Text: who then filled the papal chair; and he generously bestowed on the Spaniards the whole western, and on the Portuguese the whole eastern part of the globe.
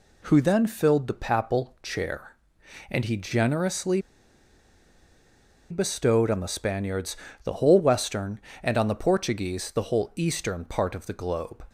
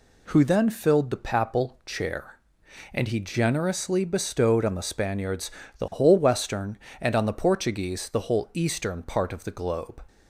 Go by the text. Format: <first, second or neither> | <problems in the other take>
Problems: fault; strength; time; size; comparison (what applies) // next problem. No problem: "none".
second | pauses between "generously" and "bestowed"; strong; at 3.9 s; 1.7 s long // pauses between "Spaniards" and "the"; slight; at 7.1 s; 0.26 s long; slight in the second